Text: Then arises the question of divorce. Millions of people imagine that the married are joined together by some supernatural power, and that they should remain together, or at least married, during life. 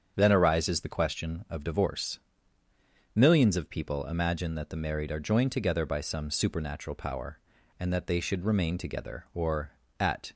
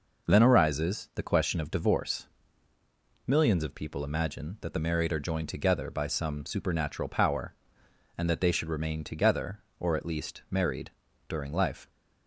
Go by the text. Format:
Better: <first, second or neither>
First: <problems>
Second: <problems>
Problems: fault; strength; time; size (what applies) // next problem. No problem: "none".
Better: second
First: starts louder than the rest; strong; until 1.1 s; 7.5 dB // stops before "least married during life"; at 10.3 s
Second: none